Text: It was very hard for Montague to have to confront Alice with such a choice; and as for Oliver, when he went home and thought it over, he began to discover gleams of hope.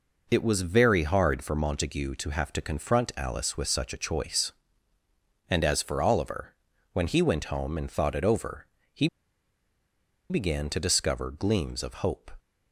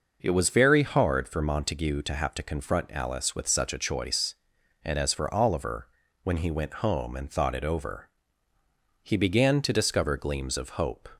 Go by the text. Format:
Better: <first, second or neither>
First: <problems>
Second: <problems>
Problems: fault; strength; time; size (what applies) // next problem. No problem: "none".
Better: second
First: pauses between "he" and "began"; at 9.0 s; 1.2 s long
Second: none